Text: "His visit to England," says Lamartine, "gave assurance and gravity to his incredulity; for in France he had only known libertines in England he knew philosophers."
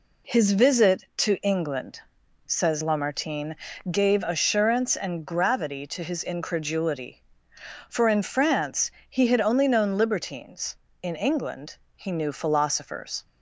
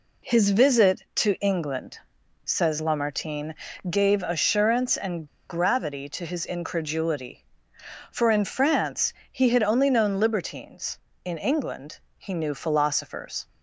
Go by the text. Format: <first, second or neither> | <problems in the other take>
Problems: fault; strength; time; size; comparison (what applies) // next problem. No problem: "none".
first | pauses between "and" and "gravity"; slight; at 5.2 s; 0.23 s long // pauses between "France" and "he"; slight; at 9.1 s; 0.20 s long; slight in the first // pauses between "England" and "he"; slight; at 11.9 s; 0.22 s long; slight in the first